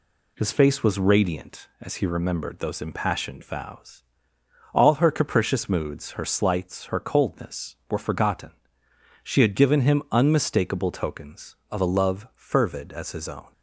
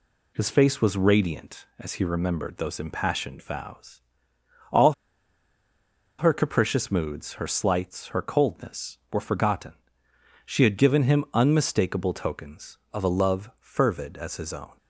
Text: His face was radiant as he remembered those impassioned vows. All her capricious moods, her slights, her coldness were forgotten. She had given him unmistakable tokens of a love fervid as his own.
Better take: first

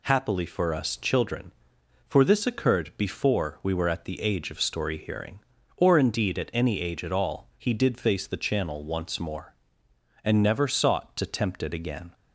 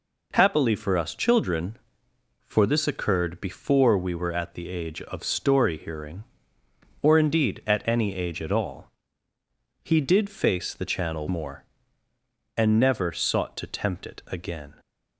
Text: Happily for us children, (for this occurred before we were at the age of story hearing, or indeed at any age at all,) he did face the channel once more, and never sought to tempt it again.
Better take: first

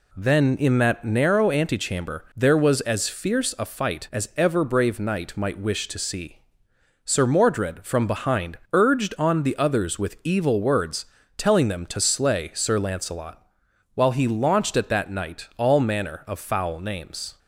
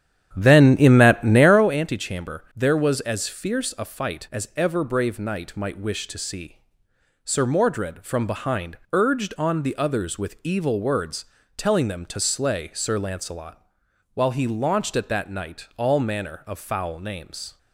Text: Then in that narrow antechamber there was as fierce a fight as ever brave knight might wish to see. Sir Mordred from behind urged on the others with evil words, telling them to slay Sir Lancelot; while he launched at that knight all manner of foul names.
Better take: first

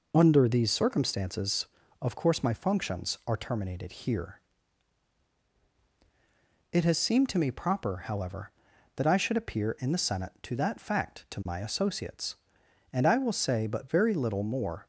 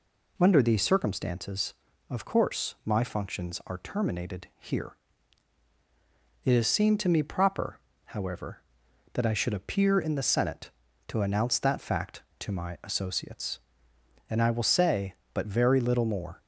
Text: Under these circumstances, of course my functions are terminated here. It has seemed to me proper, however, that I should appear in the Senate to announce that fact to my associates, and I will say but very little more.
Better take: second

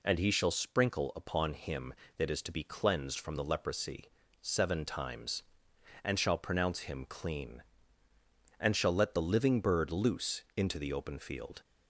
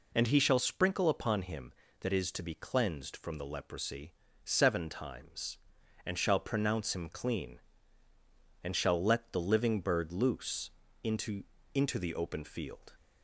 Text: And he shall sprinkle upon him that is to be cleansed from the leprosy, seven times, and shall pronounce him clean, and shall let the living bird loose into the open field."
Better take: first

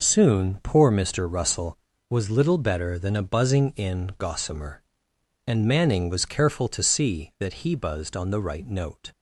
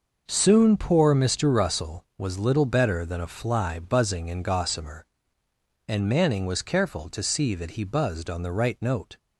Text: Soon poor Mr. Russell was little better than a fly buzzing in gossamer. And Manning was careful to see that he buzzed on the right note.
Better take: second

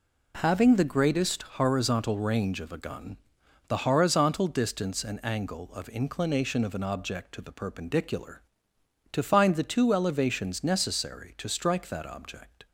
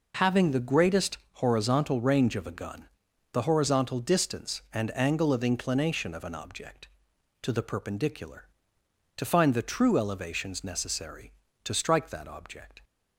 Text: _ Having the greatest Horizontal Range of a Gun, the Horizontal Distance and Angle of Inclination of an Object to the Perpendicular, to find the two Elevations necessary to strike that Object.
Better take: first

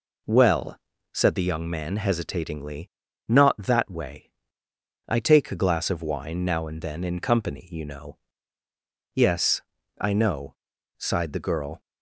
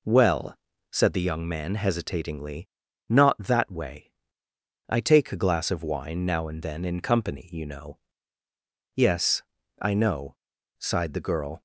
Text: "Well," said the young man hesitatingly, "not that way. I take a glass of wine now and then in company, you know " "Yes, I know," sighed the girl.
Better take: neither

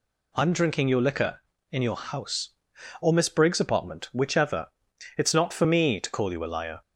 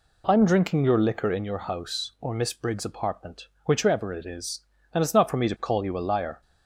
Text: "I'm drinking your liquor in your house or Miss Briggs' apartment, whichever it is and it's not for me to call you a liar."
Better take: second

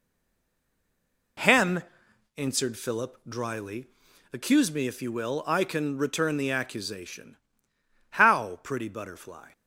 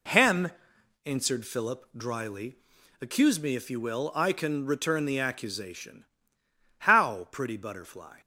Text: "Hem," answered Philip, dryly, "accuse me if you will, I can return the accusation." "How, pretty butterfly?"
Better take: second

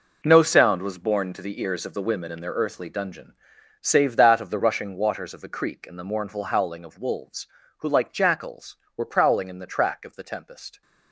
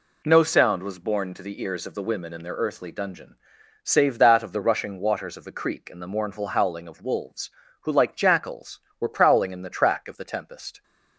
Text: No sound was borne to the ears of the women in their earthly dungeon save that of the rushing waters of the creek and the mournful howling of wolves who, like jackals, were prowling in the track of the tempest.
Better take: second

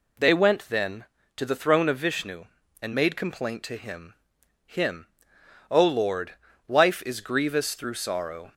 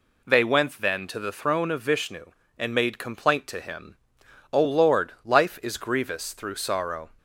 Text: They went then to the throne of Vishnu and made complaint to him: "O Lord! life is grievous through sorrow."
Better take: second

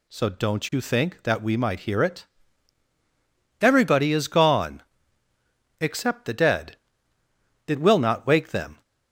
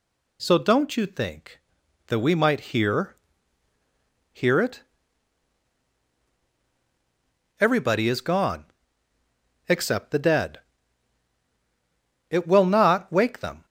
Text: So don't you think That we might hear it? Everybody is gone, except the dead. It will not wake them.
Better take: first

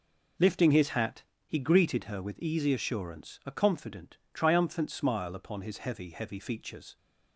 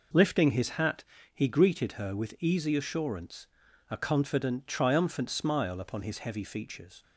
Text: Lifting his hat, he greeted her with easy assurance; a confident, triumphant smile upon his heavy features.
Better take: second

